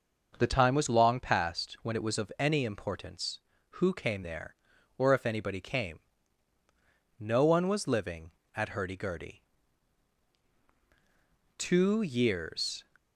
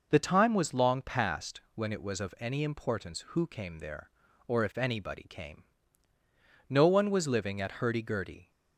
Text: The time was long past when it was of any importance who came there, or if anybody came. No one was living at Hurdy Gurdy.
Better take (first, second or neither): second